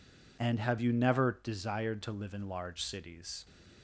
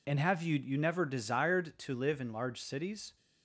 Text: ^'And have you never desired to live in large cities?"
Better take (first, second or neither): first